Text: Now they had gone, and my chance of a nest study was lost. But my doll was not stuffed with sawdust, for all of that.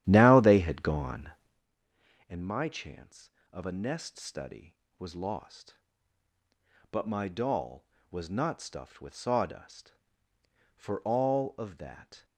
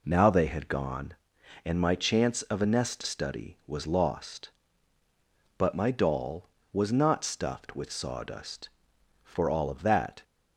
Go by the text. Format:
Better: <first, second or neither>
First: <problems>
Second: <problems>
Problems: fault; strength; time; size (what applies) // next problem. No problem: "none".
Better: second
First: starts louder than the rest; strong; until 1.7 s; 11.5 dB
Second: none